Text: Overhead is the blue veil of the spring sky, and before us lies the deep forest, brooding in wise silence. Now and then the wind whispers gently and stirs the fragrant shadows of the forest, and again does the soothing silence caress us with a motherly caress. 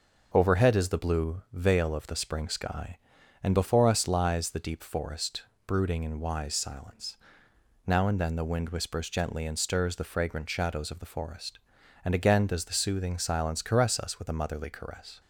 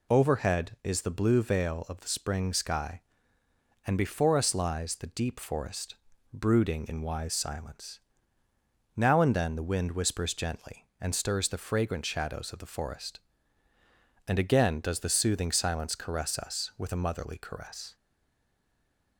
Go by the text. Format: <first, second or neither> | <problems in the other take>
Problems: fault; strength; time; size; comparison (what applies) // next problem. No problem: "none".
first | stays silent after the last word; noticeable; from 17.9 s on; 1.2 s long